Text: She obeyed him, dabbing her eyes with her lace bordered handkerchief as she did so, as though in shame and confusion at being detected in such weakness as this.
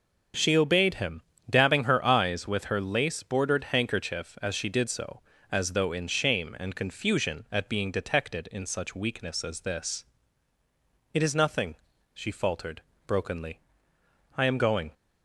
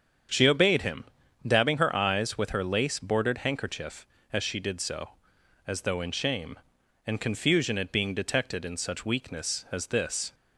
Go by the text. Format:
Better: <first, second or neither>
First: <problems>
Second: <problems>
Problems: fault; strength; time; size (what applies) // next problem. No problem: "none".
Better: second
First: starts louder than the rest; until 1.6 s; 6.5 dB // goes on to say "It is nothing she faltered brokenly I am going"; strong; from 11.1 s on; 3.8 s long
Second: starts louder than the rest; strong; until 1.7 s; 7.5 dB